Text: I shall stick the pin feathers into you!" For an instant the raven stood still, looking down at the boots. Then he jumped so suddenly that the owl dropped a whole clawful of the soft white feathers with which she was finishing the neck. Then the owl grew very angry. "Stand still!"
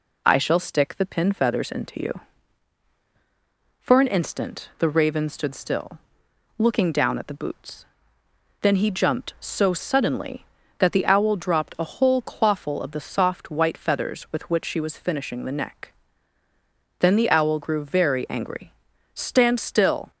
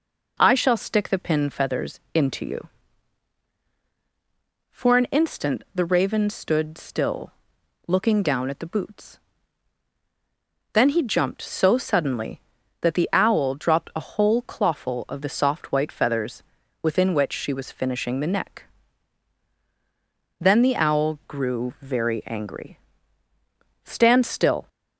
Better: first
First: none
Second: says "within" for "with"; at 16.8 s

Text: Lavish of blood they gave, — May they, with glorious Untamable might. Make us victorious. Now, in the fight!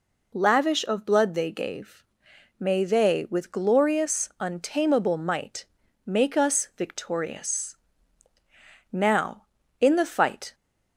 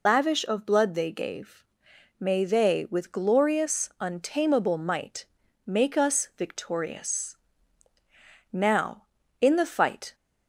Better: first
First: none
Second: loses the start of "Lavish"; at 0.0 s; 105 ms

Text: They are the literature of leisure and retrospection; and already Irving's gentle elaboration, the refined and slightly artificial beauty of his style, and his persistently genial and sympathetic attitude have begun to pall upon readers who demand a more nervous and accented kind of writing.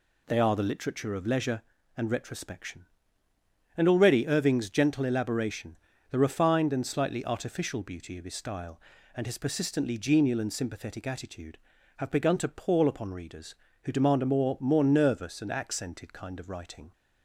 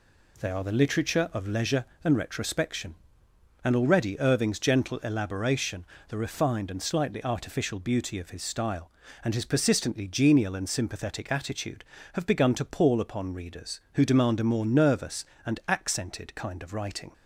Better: second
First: says "more" twice; at 14.6 s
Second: none

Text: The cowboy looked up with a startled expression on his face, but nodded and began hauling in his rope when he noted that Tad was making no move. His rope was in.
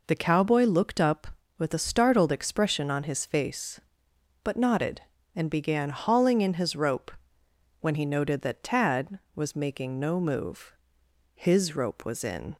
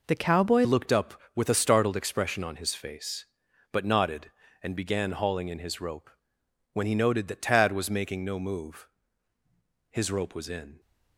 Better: first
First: pauses between "rope" and "when"; noticeable; at 7.0 s; 0.70 s long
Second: changes voice at "looked"; from 0.6 s on; 10.1 s long // pauses between "rope" and "when"; noticeable; at 6.0 s; 0.62 s long

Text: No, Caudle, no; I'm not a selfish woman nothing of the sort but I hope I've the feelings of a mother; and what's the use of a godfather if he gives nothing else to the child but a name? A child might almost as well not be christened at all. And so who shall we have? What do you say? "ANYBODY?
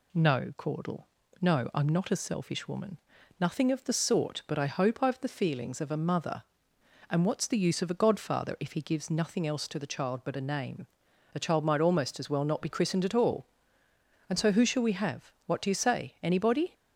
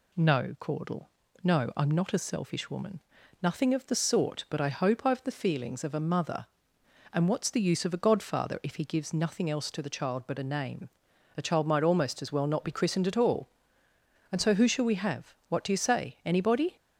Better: neither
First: pauses between "woman" and "nothing"; at 2.9 s; 0.40 s long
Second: pauses between "woman" and "nothing"; at 3.0 s; 0.40 s long

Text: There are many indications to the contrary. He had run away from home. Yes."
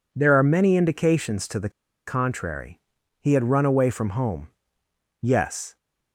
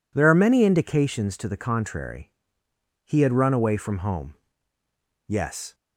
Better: second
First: pauses between "the" and "contrary"; at 1.6 s; 0.37 s long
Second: none

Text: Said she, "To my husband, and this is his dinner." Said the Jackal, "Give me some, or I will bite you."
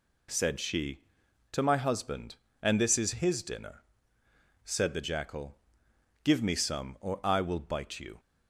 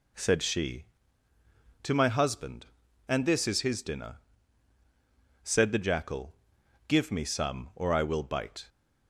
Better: first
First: none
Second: stops before "you"; at 8.6 s

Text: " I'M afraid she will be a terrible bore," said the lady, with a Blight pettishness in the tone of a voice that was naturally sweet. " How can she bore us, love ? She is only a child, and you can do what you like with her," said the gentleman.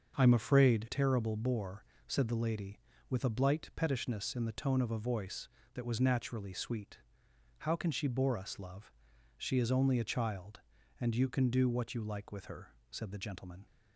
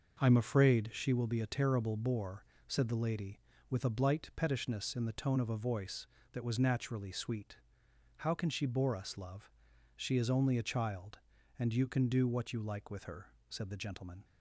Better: second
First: starts louder than the rest; until 1.1 s; 6.5 dB // skips "she will be a"; at 0.8 s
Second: none

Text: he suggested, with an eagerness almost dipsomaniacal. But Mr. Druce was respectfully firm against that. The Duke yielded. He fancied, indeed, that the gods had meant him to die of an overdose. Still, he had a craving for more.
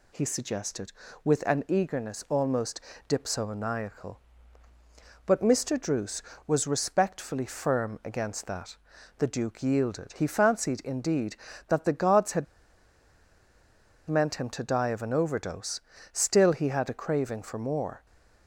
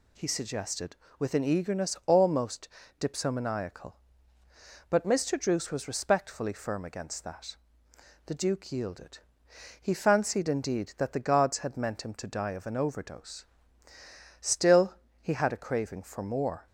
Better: second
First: pauses between "almost" and "dipsomaniacal"; slight; at 2.7 s; 0.28 s long // pauses between "had" and "meant"; strong; at 12.4 s; 1.6 s long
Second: pauses between "almost" and "dipsomaniacal"; slight; at 2.6 s; 0.30 s long

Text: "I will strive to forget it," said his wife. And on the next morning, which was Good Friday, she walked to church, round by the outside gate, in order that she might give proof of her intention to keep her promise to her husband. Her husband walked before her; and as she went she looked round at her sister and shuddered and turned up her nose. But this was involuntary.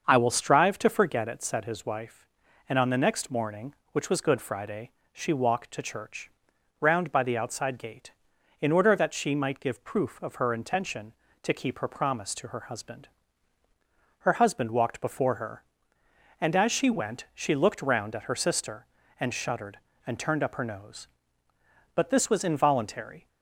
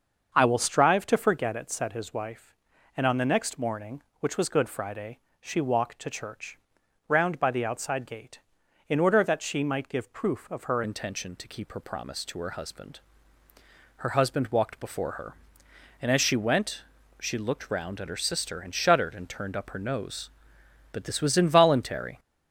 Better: first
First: starts louder than the rest; until 1.0 s; 6.5 dB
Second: starts louder than the rest; until 1.3 s; 6.5 dB // changes voice at "intention"; from 10.8 s on; 11.3 s long // pauses between "went" and "she"; at 16.8 s; 0.38 s long

